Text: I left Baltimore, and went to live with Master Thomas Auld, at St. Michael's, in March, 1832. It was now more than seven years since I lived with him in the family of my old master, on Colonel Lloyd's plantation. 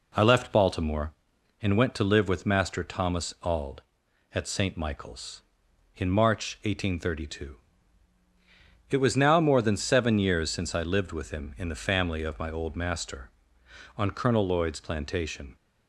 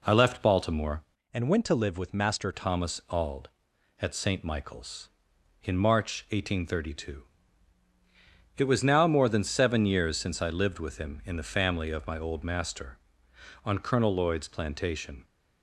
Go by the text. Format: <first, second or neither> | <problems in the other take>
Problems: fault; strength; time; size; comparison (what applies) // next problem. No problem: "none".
first | changes voice from "and" to "Master"; from 1.3 to 2.5 s; 1.2 s long